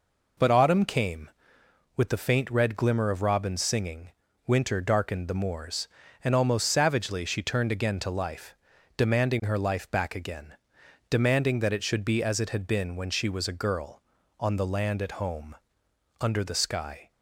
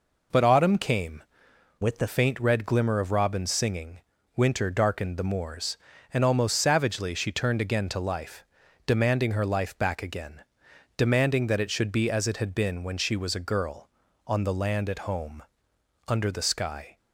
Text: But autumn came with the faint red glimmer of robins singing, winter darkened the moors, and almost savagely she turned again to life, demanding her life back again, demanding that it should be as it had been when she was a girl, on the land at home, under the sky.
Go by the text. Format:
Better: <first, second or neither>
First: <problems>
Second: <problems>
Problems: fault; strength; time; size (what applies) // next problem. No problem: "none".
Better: first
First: none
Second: changes voice from "with" to "the"; from 1.8 to 2.0 s; 0.2 s long